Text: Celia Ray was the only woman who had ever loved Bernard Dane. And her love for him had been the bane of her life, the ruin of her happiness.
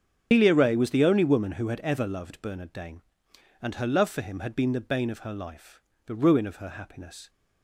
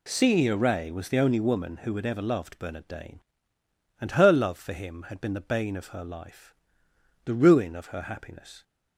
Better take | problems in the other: second | loses the start of "Celia"; at 0.3 s; 115 ms // starts louder than the rest; strong; until 1.3 s; 7.5 dB

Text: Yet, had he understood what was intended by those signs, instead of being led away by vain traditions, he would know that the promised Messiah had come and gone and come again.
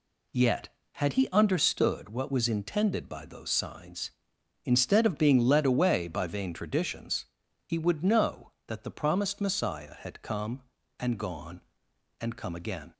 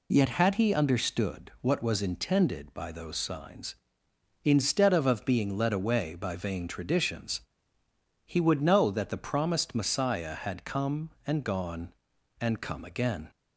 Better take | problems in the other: first | says "of" twice; at 5.0 s

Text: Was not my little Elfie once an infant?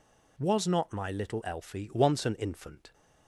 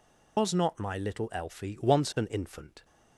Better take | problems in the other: first | loses the start of "Was"; at 0.3 s; 120 ms

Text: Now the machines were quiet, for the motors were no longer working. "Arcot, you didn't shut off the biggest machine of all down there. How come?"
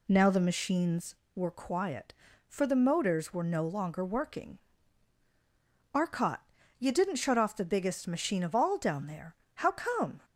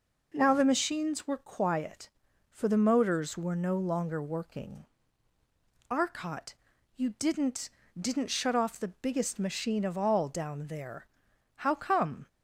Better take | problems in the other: first | says "didn't" twice; at 7.9 s

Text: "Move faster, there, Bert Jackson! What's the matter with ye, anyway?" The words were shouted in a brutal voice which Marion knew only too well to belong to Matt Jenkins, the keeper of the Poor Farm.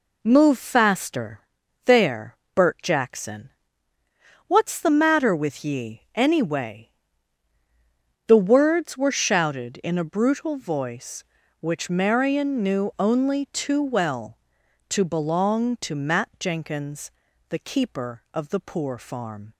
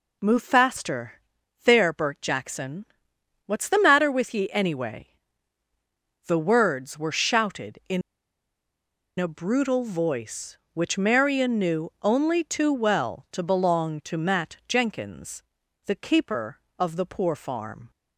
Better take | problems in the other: first | pauses between "in" and "a"; at 8.0 s; 1.1 s long

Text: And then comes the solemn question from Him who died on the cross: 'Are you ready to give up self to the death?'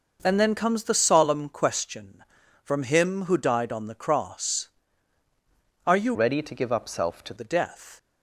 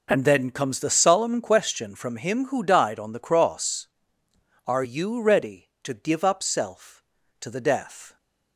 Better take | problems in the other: second | changes voice from "ready" to "to"; from 6.1 to 7.3 s; 1.2 s long

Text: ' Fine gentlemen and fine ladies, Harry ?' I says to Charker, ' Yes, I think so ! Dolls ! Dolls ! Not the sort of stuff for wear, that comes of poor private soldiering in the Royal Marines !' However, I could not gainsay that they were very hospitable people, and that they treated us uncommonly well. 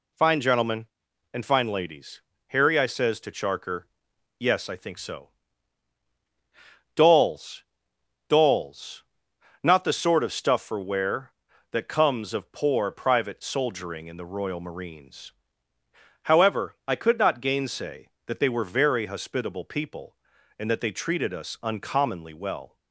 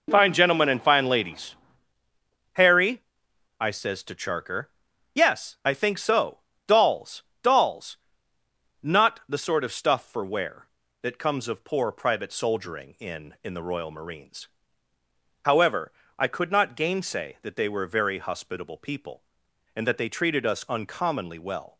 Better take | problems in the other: first | says "in" twice; at 13.4 s

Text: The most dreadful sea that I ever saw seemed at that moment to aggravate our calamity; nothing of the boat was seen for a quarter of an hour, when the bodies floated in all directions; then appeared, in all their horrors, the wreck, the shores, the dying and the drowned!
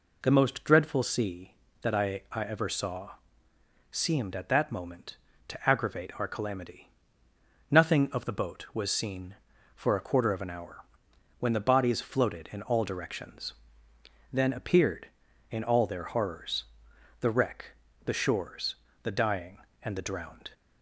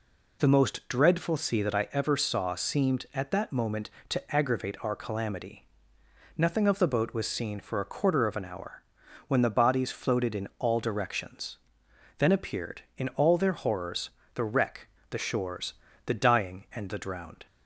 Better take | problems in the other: second | says "I" twice; at 2.3 s // pauses between "saw" and "seemed"; noticeable; at 3.1 s; 0.78 s long

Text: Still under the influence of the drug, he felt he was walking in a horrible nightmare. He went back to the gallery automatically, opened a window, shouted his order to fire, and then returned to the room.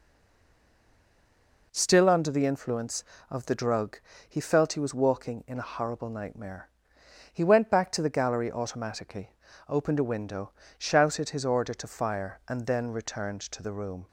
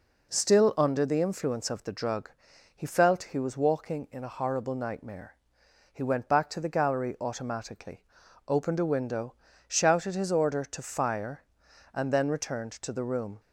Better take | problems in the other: second | stays silent before the first word; noticeable; until 1.7 s; 1.7 s long

